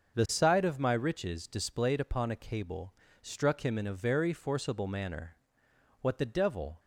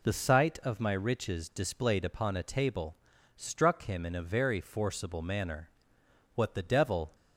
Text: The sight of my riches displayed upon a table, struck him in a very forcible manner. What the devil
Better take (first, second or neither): second